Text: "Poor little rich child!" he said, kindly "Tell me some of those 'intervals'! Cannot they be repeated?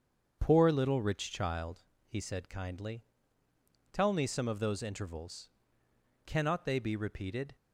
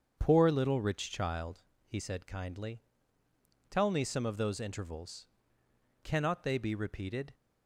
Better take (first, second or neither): neither